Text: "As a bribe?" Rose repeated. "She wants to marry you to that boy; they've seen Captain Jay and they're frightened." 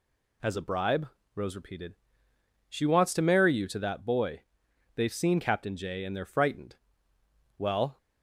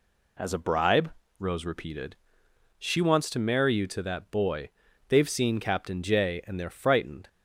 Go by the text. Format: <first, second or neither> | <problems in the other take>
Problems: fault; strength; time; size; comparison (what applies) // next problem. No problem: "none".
second | goes on to say "Well"; slight; from 7.5 s on; 0.40 s long